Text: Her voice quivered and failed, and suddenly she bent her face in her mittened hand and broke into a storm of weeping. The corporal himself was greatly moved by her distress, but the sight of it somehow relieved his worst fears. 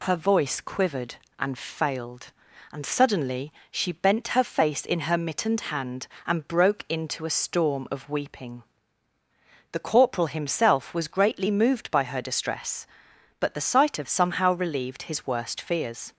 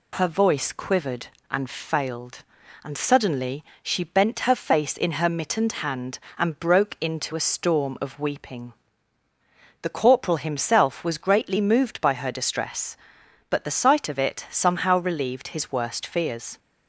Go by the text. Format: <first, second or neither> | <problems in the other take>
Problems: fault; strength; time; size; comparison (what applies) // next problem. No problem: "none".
second | pauses between "suddenly" and "she"; slight; at 3.5 s; 0.18 s long; slight in the second // skips "it"; at 14.0 s